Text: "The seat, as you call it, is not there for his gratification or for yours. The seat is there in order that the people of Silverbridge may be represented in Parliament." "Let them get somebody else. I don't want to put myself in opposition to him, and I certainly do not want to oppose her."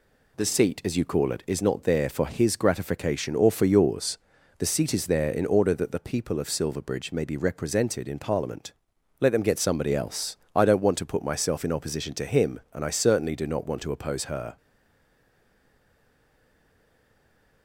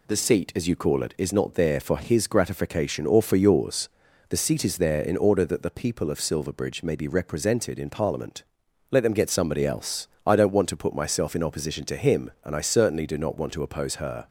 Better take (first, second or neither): second